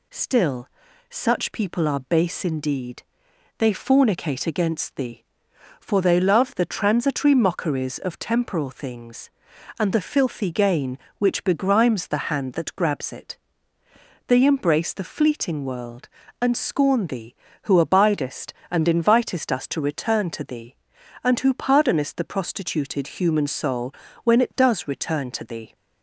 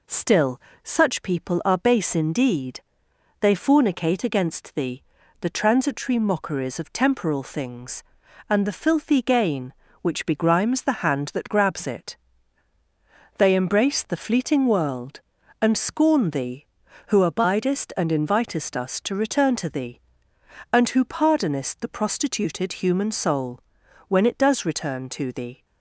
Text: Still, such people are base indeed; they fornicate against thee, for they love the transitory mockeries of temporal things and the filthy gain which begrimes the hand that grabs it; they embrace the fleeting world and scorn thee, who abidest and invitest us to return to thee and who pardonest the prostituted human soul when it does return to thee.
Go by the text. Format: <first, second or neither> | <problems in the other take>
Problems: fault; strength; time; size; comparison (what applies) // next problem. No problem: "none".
first | skips "for they love"; at 5.2 s // pauses between "soul" and "when"; noticeable; at 23.5 s; 0.48 s long; slight in the first